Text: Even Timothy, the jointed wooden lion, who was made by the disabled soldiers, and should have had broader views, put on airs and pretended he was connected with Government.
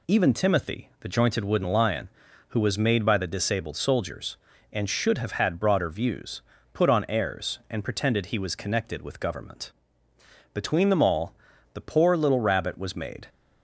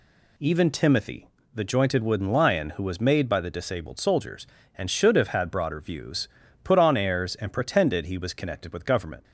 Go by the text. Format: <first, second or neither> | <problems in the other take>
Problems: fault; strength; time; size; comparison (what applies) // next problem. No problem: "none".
second | goes on to say "Between them all the poor little Rabbit was made"; strong; from 10.5 s on; 2.7 s long